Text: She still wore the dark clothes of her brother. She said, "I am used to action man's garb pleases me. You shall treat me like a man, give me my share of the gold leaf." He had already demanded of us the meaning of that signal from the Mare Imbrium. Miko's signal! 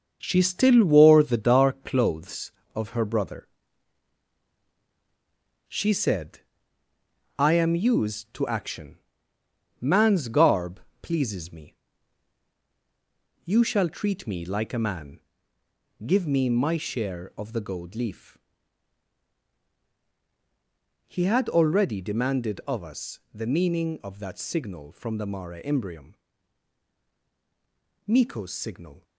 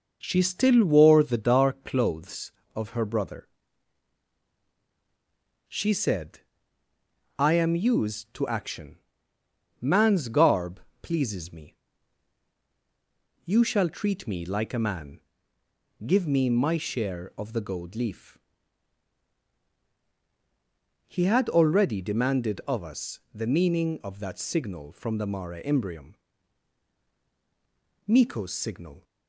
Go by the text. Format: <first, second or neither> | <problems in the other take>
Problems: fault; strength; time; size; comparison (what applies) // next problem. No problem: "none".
second | gets quieter; throughout; 7 dB // pauses between "action" and "man's"; noticeable; at 8.9 s; 0.82 s long; noticeable in the second // pauses between "garb" and "pleases"; slight; at 10.7 s; 0.22 s long; slight in the second // pauses between "us" and "the"; slight; at 23.1 s; 0.16 s long; slight in the second